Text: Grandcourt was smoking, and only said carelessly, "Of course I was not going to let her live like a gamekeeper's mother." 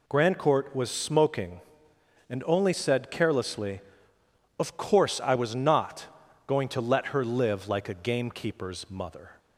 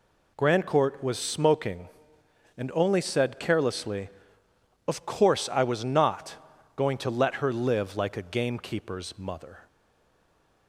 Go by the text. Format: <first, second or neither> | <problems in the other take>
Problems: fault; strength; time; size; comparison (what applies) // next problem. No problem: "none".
first | pauses between "not" and "going"; at 6.3 s; 0.40 s long; also in the first // stays silent after the last word; from 9.6 s on; 1.0 s long